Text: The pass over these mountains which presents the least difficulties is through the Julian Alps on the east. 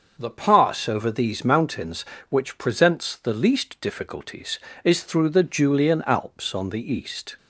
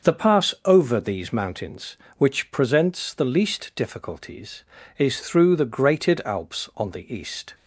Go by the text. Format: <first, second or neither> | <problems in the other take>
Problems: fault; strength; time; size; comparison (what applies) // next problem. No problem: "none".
first | starts louder than the rest; until 1.1 s; 6 dB; also in the first // says "Grated" for "Julian"; at 5.6 s